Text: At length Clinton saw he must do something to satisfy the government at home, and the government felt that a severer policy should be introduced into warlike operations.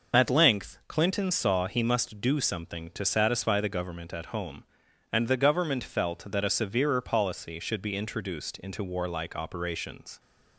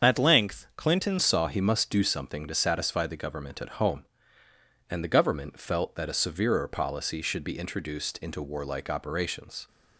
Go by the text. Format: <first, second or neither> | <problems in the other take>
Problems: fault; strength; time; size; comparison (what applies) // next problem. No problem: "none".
first | starts louder than the rest; strong; until 1.1 s; 7.5 dB // changes voice at "saw"; from 1.1 s on; 8.5 s long